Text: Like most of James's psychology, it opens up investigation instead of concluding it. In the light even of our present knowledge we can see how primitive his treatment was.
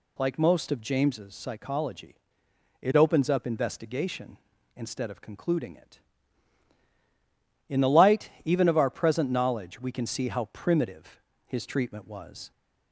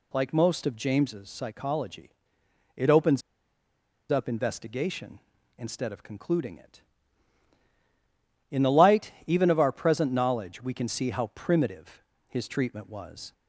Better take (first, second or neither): first